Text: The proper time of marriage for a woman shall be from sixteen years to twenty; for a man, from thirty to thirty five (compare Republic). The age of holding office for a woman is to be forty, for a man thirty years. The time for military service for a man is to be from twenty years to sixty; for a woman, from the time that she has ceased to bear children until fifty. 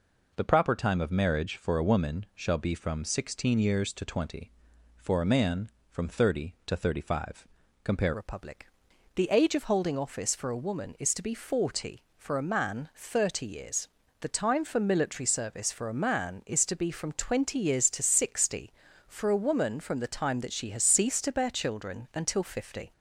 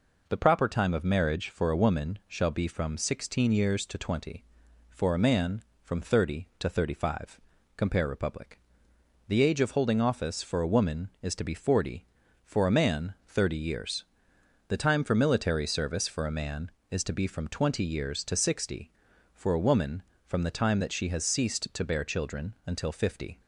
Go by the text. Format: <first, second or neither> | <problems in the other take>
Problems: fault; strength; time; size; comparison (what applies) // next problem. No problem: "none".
second | changes voice at "Republic"; from 8.1 s on; 14.8 s long